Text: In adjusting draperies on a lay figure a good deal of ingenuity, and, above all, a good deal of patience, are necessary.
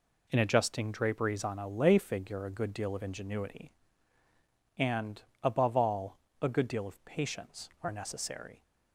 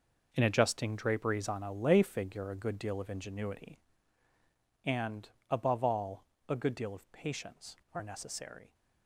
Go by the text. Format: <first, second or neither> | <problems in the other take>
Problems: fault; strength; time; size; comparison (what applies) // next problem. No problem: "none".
first | gets quieter; strong; throughout; 11 dB